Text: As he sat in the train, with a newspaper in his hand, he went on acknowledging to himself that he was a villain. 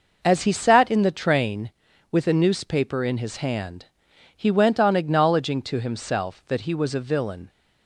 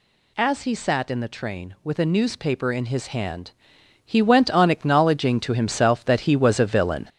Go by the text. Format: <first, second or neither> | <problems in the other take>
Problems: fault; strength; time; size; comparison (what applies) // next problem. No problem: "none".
first | gets louder; throughout; 6.5 dB